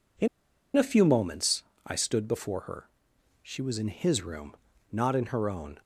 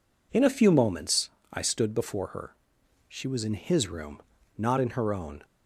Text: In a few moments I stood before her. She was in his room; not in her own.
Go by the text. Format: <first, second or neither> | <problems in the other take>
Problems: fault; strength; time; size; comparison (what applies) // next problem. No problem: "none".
second | pauses between "In" and "a"; noticeable; at 0.2 s; 0.48 s long // pauses between "moments" and "I"; slight; at 1.6 s; 0.20 s long; slight in the second